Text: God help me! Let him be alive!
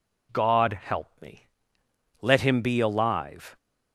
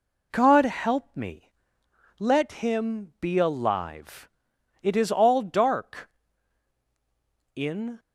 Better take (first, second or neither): first